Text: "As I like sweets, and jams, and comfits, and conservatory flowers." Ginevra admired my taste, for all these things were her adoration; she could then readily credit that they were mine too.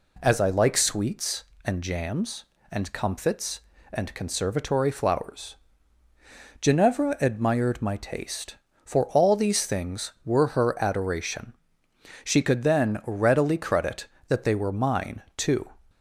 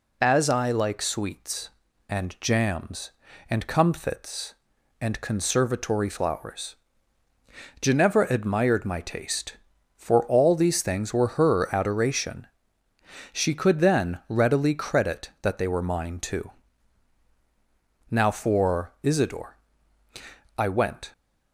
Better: first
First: none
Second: goes on to say "Now for Isidore I went"; strong; from 18.1 s on; 3.0 s long

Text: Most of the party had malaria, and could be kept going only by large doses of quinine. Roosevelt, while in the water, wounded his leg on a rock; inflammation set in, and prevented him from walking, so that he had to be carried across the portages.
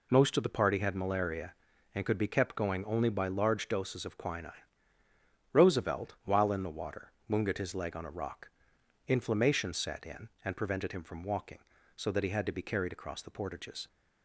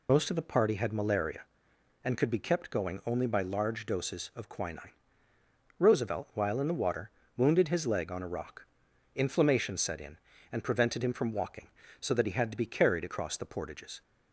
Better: first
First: none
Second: loses the start of "Most"; at 0.0 s; 45 ms

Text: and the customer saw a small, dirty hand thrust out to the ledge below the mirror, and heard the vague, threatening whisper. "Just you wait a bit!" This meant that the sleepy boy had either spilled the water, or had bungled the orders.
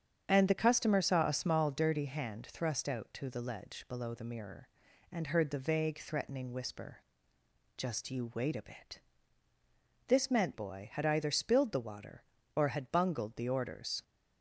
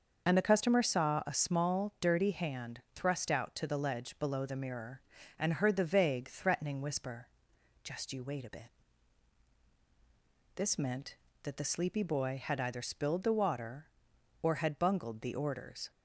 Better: second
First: starts louder than the rest; strong; until 1.2 s; 8 dB // skips "that the sleepy"; at 10.5 s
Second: starts louder than the rest; until 1.3 s; 6.5 dB

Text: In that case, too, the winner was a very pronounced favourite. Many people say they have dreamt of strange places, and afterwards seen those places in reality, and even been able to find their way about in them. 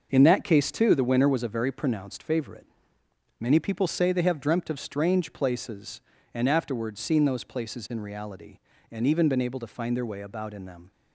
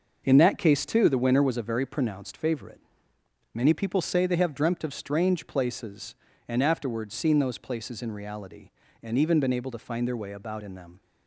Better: neither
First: starts louder than the rest; noticeable; until 1.1 s; 6 dB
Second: starts louder than the rest; noticeable; until 1.2 s; 6 dB

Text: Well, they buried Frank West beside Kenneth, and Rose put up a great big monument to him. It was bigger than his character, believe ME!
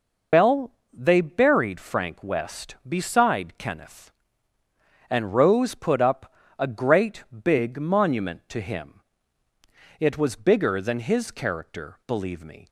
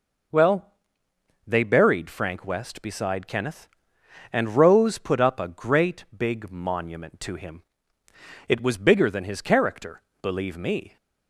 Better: second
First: loses the start of "Well"; at 0.3 s; 105 ms // pauses between "up" and "a"; slight; at 6.3 s; 0.26 s long // pauses between "great" and "big"; slight; at 7.2 s; 0.22 s long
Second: none

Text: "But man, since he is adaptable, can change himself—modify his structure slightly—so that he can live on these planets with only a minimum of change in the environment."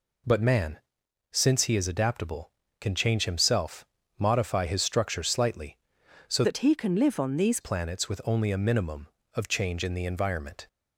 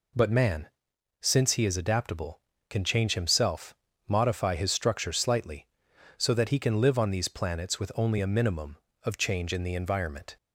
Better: second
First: changes voice from "that" to "these"; from 6.4 to 7.5 s; 1.1 s long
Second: none

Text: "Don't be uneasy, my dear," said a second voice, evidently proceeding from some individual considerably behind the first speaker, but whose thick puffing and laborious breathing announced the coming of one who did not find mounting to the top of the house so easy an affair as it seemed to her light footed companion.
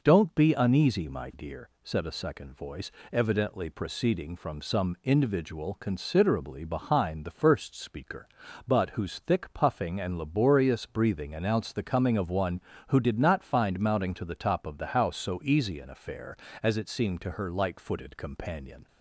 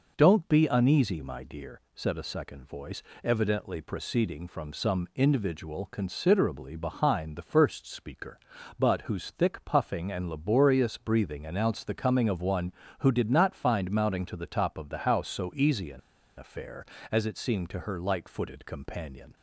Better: first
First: none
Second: pauses between "an" and "affair"; at 15.9 s; 0.37 s long

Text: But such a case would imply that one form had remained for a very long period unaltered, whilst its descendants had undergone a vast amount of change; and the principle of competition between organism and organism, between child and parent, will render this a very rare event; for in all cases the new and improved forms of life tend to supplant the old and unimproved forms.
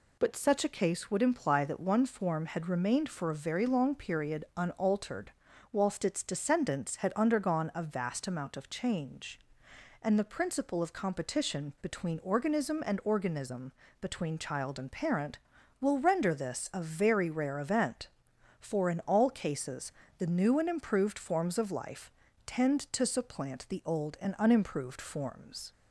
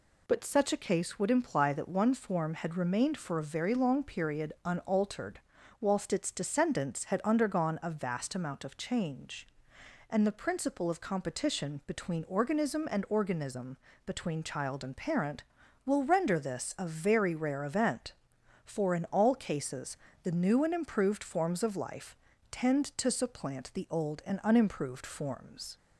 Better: neither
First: pauses between "cases" and "the"; slight; at 19.9 s; 0.28 s long // pauses between "life" and "tend"; slight; at 22.1 s; 0.34 s long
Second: pauses between "cases" and "the"; slight; at 19.9 s; 0.28 s long // pauses between "life" and "tend"; slight; at 22.1 s; 0.34 s long

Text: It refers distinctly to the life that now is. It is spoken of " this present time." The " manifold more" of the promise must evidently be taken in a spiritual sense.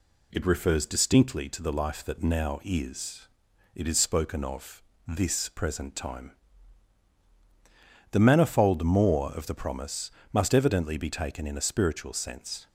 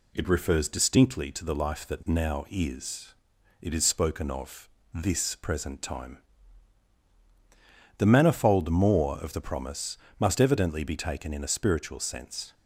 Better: neither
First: pauses between "promise" and "must"; slight; at 10.1 s; 0.20 s long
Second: pauses between "promise" and "must"; slight; at 9.9 s; 0.20 s long

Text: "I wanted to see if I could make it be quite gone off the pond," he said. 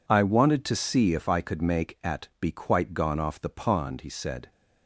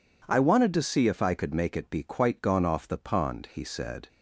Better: second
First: says "at" for "it"; at 2.0 s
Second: none

